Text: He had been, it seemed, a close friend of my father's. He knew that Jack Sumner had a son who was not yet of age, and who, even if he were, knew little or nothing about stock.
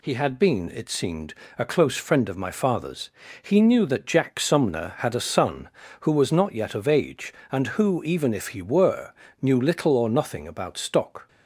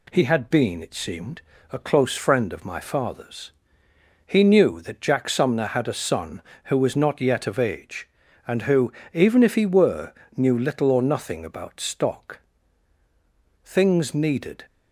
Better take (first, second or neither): first